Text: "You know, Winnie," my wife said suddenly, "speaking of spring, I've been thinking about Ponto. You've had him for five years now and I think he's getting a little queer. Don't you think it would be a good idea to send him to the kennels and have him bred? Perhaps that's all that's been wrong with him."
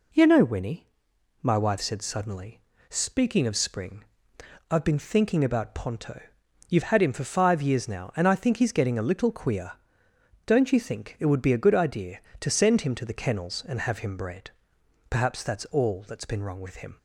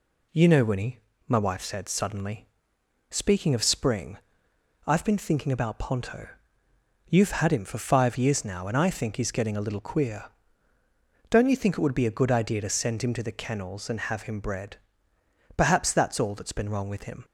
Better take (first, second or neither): neither